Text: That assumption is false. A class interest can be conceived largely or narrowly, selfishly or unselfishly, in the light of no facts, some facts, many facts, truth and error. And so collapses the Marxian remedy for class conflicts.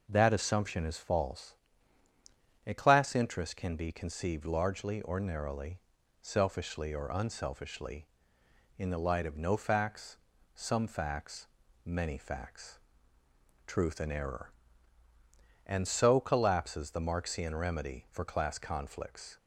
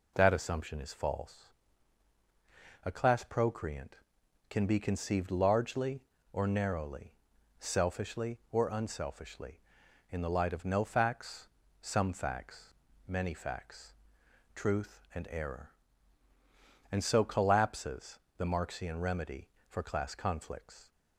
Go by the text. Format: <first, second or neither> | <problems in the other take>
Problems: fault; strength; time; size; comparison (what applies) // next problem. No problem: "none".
first | says "procreant" for "interest"; at 3.2 s // pauses between "collapses" and "the"; slight; at 18.1 s; 0.18 s long